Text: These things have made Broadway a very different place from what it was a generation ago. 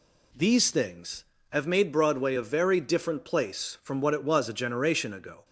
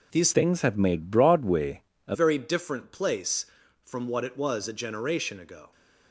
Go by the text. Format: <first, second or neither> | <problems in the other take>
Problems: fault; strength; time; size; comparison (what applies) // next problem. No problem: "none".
first | changes voice from "things" to "a"; from 0.3 to 2.1 s; 1.8 s long // pauses between "Broadway" and "a"; slight; at 1.8 s; 0.26 s long